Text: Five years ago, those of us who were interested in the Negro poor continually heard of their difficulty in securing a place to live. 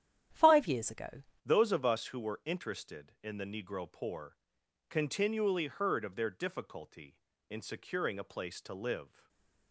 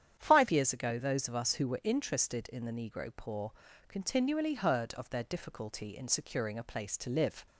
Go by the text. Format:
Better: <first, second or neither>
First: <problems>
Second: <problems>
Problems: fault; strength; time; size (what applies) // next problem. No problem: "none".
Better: second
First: starts louder than the rest; strong; until 1.5 s; 10 dB // changes voice at "those"; from 1.4 s on; 7.8 s long // pauses between "poor" and "continually"; noticeable; at 4.3 s; 0.54 s long // stays silent after the last word; slight; from 9.0 s on; 0.7 s long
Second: starts louder than the rest; strong; until 1.2 s; 9 dB // pauses between "poor" and "continually"; slight; at 3.5 s; 0.36 s long